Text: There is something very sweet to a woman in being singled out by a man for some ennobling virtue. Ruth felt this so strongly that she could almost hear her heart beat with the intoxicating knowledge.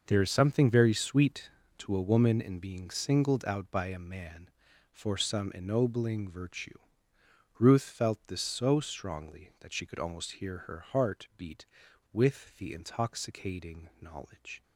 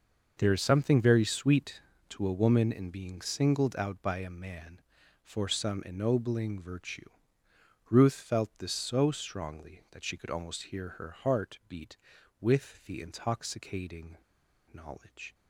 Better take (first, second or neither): first